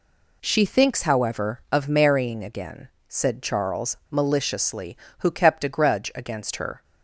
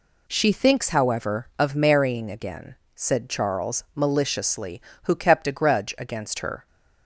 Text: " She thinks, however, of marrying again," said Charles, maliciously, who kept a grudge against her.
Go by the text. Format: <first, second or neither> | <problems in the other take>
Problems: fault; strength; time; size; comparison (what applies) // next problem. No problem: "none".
neither | none